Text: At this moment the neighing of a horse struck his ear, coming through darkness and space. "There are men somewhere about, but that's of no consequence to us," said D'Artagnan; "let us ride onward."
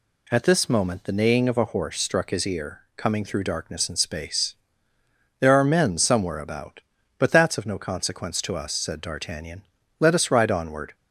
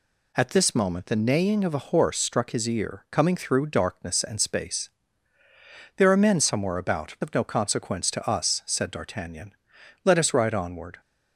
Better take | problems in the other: first | skips "but that's"; at 7.1 s

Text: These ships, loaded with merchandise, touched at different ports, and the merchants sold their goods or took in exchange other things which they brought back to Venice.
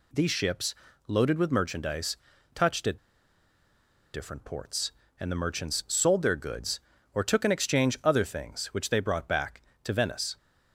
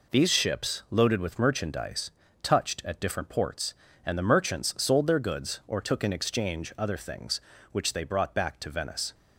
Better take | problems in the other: second | pauses between "at" and "different"; at 2.9 s; 1.1 s long

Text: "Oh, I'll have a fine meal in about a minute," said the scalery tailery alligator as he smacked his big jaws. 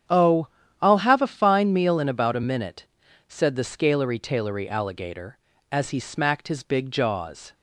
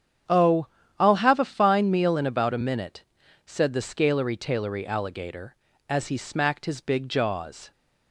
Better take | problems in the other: neither | starts louder than the rest; strong; the same in both

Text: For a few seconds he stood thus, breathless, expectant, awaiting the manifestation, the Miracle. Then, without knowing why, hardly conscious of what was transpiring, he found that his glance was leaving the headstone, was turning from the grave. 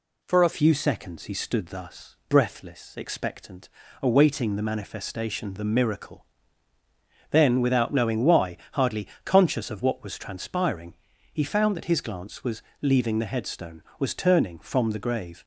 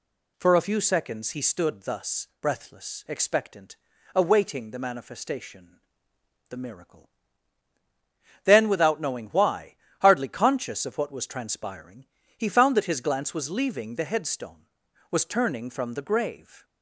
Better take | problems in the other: second | changes voice at "few"; from 0.5 s on; 14.9 s long // pauses between "hardly" and "conscious"; slight; at 9.0 s; 0.16 s long // pauses between "was" and "leaving"; slight; at 12.6 s; 0.20 s long

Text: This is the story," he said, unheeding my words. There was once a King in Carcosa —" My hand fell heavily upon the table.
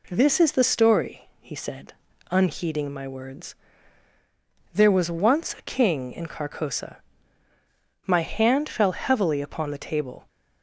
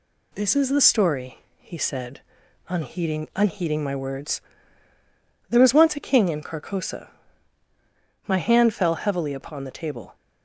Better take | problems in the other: first | says "unheeding" twice; at 3.3 s

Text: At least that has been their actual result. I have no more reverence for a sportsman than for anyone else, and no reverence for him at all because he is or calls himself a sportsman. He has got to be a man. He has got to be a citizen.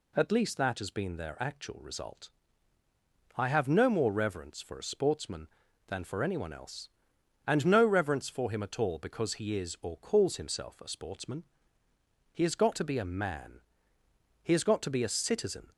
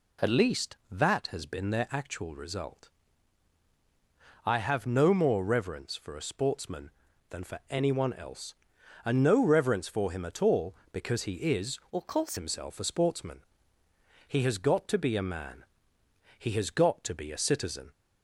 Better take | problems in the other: first | changes voice from "or" to "calls"; from 11.9 to 12.3 s; 0.4 s long

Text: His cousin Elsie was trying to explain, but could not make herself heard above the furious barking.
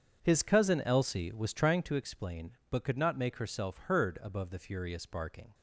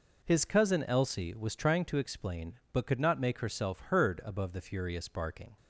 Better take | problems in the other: second | starts louder than the rest; strong; until 2.0 s; 7.5 dB

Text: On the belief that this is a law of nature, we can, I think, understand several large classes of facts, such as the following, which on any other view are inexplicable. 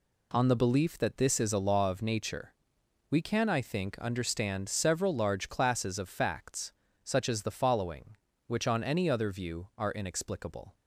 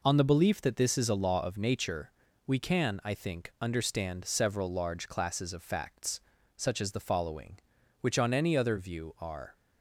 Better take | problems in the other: first | stops before "inexplicable"; at 9.5 s

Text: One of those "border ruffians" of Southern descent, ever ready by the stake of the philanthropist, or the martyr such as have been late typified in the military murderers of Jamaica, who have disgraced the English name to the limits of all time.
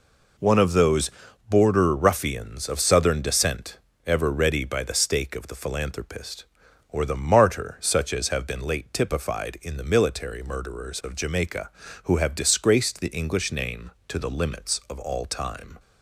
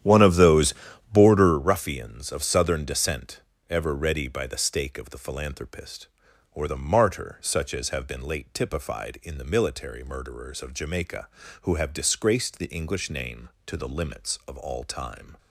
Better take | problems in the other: first | starts louder than the rest; strong; until 1.6 s; 10.5 dB // pauses between "those" and "border"; at 0.7 s; 0.40 s long; also in the first

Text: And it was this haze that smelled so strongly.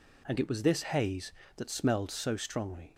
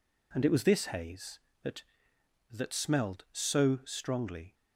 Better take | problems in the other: first | says "that" twice; at 2.5 s

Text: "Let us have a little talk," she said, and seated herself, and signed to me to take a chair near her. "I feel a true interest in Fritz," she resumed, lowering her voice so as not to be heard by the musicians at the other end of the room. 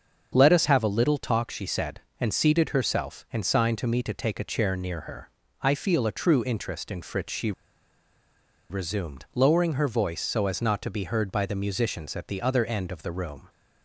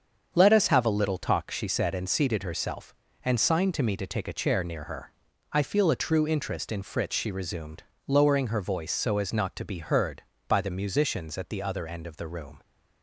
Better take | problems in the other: second | starts louder than the rest; until 1.3 s; 7 dB; strong in the second // pauses between "she" and "resumed"; at 7.5 s; 1.1 s long

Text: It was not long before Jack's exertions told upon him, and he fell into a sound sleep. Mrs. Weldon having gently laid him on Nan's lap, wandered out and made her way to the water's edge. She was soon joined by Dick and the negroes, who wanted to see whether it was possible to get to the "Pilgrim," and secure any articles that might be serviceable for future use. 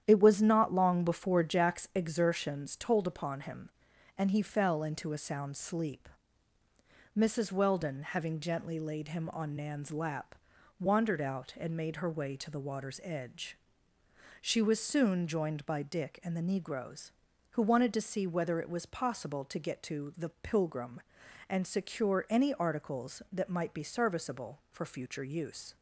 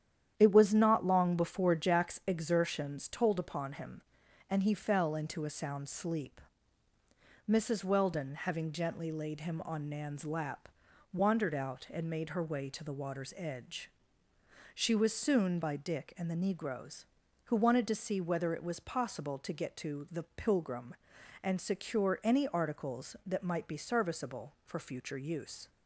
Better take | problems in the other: first | starts louder than the rest; strong; until 1.3 s; 10 dB; strong in the first // skips "joined"; at 15.6 s

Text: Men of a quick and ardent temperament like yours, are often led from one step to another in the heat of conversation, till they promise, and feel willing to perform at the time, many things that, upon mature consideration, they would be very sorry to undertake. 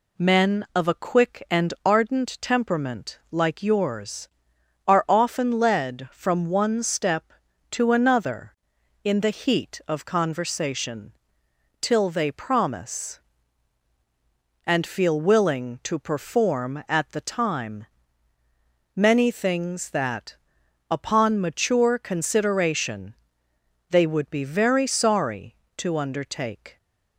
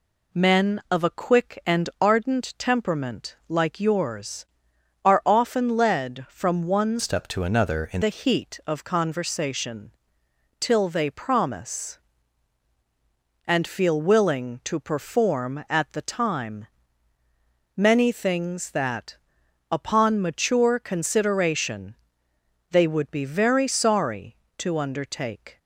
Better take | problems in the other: first | changes voice from "step" to "in"; from 6.9 to 8.0 s; 1.1 s long

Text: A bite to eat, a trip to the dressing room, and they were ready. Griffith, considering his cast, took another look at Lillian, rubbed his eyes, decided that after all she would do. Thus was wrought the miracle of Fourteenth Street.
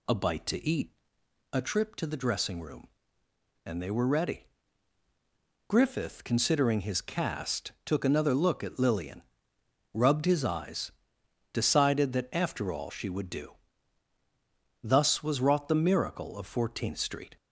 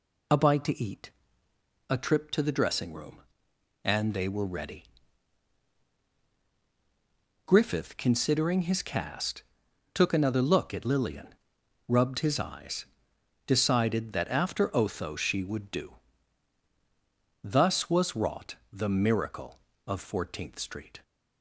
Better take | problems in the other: first | says "otho" for "all"; at 14.7 s // pauses between "wrought" and "the"; slight; at 18.5 s; 0.16 s long

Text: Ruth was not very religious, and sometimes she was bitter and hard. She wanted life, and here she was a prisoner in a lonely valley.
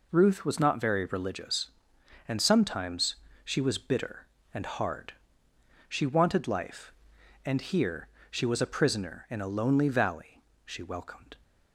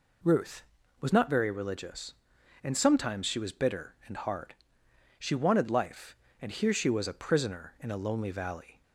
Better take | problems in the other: second | pauses between "sometimes" and "she"; slight; at 3.1 s; 0.28 s long // pauses between "here" and "she"; slight; at 8.0 s; 0.24 s long // goes on to say "She welcomed"; noticeable; from 10.6 s on; 0.70 s long

